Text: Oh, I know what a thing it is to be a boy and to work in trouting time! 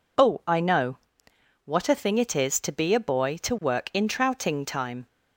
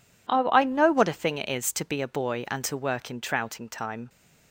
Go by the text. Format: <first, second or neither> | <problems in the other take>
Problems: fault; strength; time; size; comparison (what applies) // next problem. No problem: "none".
second | pauses between "know" and "what"; noticeable; at 0.9 s; 0.70 s long // skips "and"; at 3.3 s